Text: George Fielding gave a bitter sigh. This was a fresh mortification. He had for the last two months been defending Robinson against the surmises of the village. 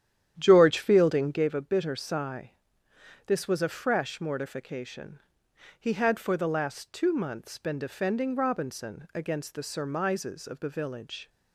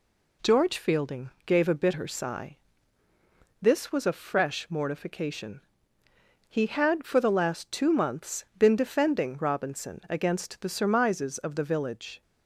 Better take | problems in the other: second | starts louder than the rest; strong; until 1.5 s; 10 dB

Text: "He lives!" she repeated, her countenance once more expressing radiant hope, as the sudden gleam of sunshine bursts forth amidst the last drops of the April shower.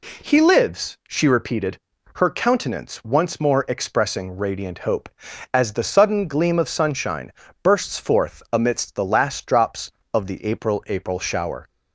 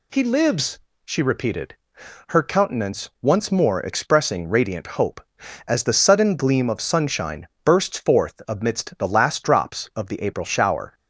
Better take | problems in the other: second | pauses between "sunshine" and "bursts"; slight; at 7.3 s; 0.30 s long; slight in the second // says "April" twice; at 10.8 s

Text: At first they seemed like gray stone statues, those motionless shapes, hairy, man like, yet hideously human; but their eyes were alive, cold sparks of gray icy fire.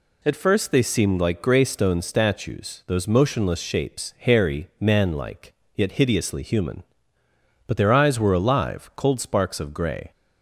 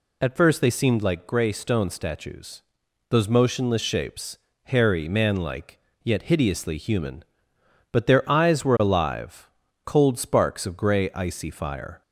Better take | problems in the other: second | stops before "icy fire"; at 10.1 s

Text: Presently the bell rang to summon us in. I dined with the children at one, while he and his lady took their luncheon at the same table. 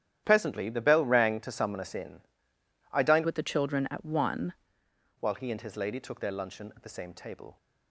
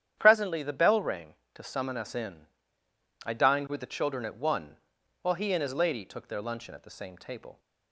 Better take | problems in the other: second | starts louder than the rest; strong; until 1.2 s; 11 dB; strong in the second // changes voice from "with" to "one"; from 3.2 to 4.5 s; 1.3 s long

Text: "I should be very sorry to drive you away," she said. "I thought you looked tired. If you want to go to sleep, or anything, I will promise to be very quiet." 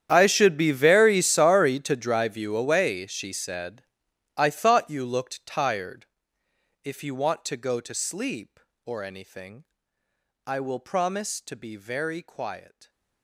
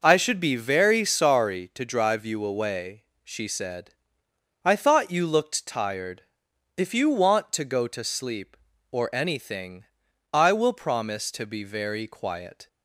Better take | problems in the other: second | gets quieter; strong; throughout; 20.5 dB

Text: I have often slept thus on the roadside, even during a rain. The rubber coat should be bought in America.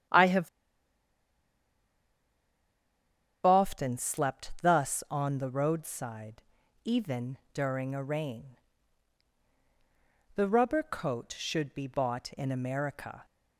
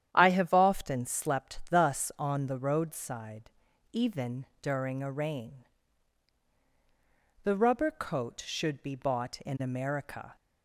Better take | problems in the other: second | starts louder than the rest; strong; until 4.0 s; 10 dB; strong in the second // pauses between "have" and "often"; strong; at 0.4 s; 2.9 s long // pauses between "even" and "during"; slight; at 7.3 s; 0.16 s long; slight in the second

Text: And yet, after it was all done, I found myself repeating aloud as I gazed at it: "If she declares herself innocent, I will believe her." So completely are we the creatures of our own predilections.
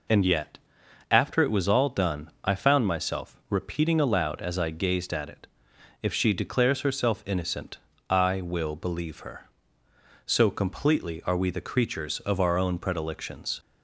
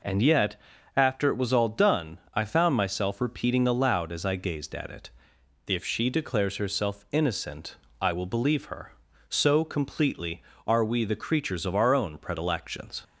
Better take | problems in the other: neither | none

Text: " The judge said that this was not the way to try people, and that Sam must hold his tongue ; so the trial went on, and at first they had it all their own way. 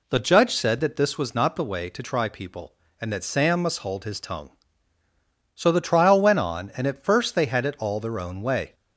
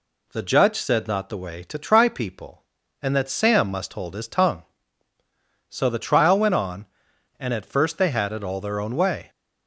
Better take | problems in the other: first | skips "that this was"; at 1.0 s

